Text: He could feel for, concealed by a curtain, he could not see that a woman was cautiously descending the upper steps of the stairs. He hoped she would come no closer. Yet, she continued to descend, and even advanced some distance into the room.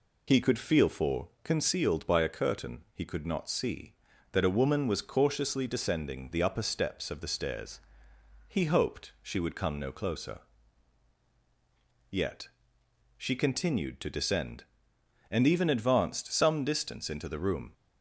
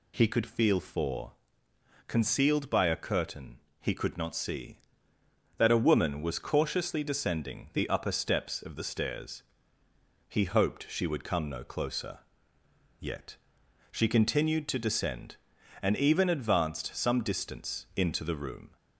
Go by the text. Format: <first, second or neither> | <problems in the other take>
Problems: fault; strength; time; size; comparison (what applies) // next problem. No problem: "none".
second | loses the start of "He"; at 0.2 s; 40 ms